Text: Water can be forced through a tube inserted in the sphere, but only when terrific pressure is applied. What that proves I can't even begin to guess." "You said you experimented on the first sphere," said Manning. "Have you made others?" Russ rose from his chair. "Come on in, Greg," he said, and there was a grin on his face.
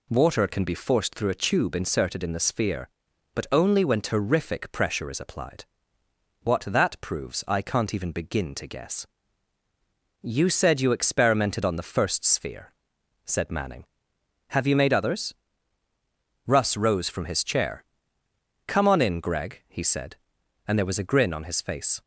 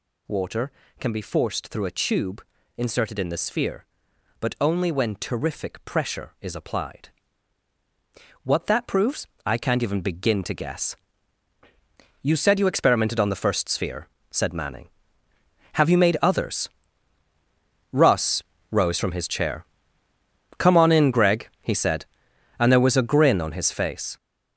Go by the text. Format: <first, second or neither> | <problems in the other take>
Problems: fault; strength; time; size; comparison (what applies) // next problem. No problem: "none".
first | gets louder; strong; throughout; 9 dB // pauses between "tube" and "inserted"; slight; at 2.4 s; 0.34 s long // pauses between "proves" and "I"; slight; at 9.2 s; 0.18 s long // pauses between "Russ" and "rose"; slight; at 18.4 s; 0.29 s long